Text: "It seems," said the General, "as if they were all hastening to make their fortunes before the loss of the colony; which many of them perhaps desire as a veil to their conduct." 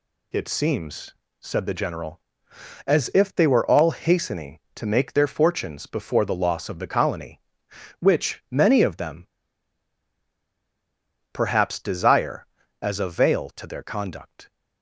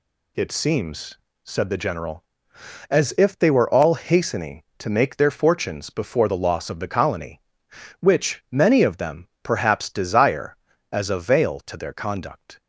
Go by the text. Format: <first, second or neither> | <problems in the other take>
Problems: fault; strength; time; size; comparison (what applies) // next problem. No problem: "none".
second | pauses between "them" and "perhaps"; strong; at 9.2 s; 2.0 s long